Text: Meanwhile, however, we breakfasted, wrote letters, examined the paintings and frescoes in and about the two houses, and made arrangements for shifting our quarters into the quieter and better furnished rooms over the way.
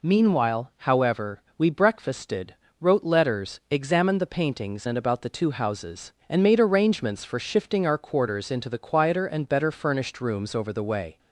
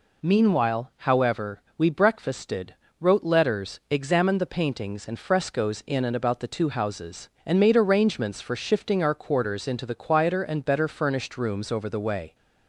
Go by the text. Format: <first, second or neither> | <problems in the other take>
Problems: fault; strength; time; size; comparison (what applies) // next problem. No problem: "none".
second | skips "and frescoes in"; at 4.8 s